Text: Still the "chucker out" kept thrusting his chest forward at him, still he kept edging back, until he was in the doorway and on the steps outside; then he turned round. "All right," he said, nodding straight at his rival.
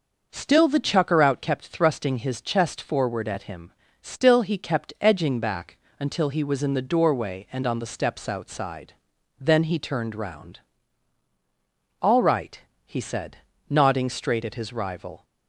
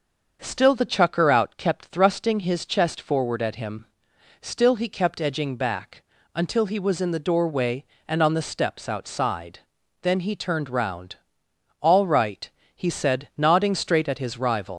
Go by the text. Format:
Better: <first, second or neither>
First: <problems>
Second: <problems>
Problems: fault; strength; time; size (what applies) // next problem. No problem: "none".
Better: first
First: starts louder than the rest; noticeable; until 1.3 s; 6 dB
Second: starts louder than the rest; until 1.4 s; 6.5 dB // leaves "rival" unfinished; at 14.7 s; 130 ms